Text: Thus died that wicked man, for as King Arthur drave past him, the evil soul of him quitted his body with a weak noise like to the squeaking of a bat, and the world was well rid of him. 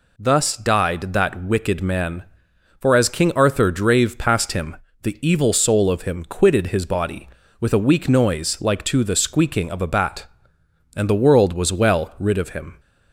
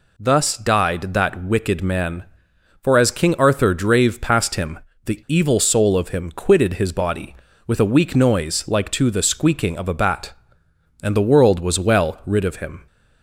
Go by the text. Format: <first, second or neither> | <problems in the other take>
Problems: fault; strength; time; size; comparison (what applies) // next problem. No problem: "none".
neither | none